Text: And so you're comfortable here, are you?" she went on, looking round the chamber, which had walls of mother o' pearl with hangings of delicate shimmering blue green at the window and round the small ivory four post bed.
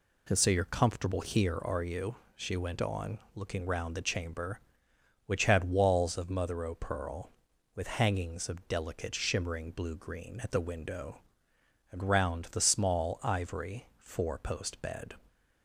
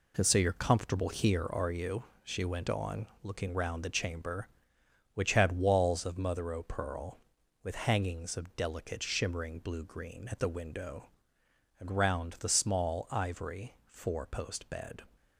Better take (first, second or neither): first